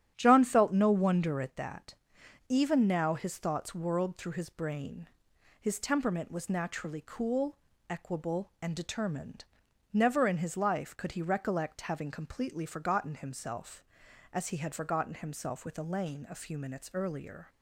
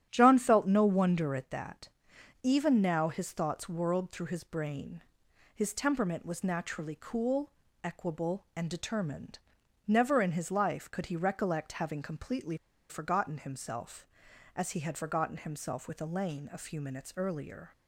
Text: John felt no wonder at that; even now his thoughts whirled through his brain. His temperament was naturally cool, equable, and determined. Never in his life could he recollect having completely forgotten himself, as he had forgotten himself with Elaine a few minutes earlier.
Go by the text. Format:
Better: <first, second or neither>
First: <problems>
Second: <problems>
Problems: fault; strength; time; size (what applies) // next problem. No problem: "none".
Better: first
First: starts louder than the rest; strong; until 1.1 s; 10.5 dB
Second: starts louder than the rest; strong; until 1.1 s; 10.5 dB // pauses between "completely" and "forgotten"; slight; at 12.5 s; 0.33 s long